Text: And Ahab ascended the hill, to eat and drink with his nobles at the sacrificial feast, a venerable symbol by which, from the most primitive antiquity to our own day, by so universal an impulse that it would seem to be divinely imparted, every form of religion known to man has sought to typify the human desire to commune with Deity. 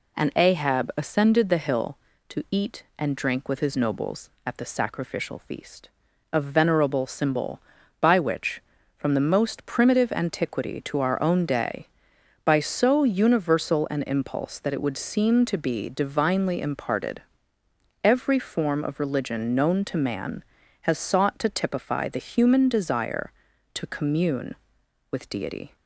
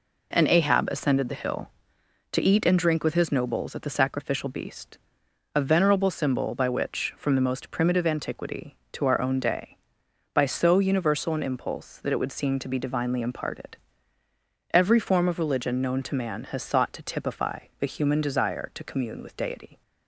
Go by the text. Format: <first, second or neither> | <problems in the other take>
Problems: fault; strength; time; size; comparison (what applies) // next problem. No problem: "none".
first | says "beast" for "feast"; at 4.4 s // pauses between "typify" and "the"; slight; at 17.5 s; 0.22 s long